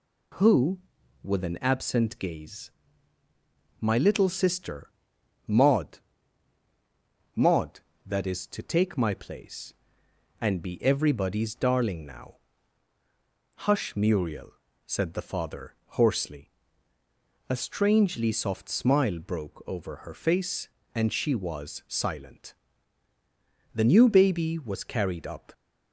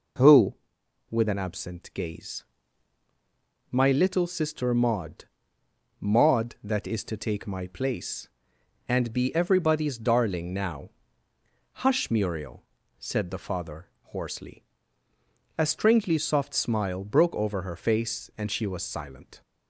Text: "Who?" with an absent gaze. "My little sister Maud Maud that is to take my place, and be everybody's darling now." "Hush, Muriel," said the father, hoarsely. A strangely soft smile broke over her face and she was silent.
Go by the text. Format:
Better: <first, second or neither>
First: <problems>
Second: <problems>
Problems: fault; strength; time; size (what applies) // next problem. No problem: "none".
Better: second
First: pauses between "sister" and "Maud"; noticeable; at 4.9 s; 0.56 s long // pauses between "Maud" and "Maud"; strong; at 5.9 s; 1.3 s long // goes on to say "The new baby was carried up"; strong; from 23.7 s on; 1.7 s long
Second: pauses between "Maud" and "Maud"; noticeable; at 5.2 s; 0.76 s long